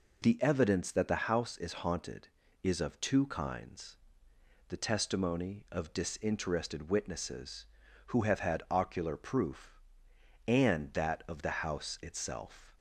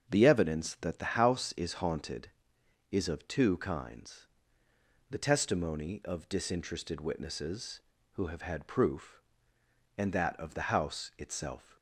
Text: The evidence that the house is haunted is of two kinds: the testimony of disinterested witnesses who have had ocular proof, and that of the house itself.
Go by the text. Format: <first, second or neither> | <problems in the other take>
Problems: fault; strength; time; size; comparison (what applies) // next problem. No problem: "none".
first | starts louder than the rest; strong; until 1.1 s; 7 dB // skips "ocular"; at 8.6 s